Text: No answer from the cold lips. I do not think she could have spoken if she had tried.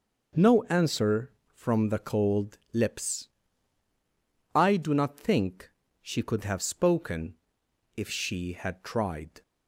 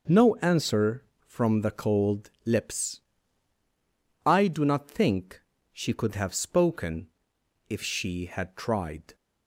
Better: neither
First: pauses between "think" and "she"; slight; at 5.6 s; 0.32 s long // pauses between "spoken" and "if"; noticeable; at 7.3 s; 0.64 s long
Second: pauses between "think" and "she"; slight; at 5.4 s; 0.32 s long // pauses between "spoken" and "if"; noticeable; at 7.0 s; 0.64 s long

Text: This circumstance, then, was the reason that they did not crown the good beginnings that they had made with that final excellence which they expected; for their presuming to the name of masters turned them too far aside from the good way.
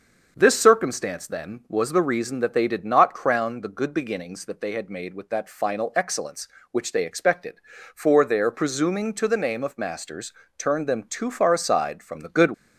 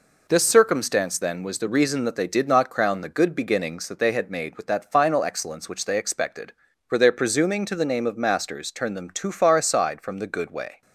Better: second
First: starts louder than the rest; until 1.3 s; 6.5 dB // pauses between "masters" and "turned"; slight; at 10.3 s; 0.24 s long // stops before "way"; at 12.5 s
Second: none

